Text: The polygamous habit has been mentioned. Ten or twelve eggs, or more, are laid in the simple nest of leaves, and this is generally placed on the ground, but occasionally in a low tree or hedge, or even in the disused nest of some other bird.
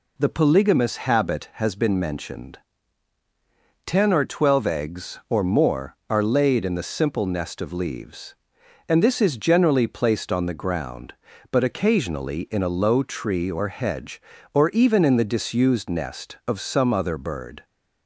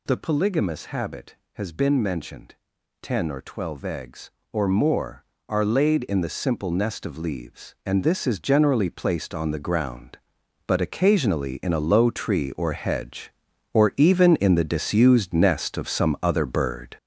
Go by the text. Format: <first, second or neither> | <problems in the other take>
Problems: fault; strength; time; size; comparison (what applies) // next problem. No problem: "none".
first | gets louder; noticeable; throughout; 6 dB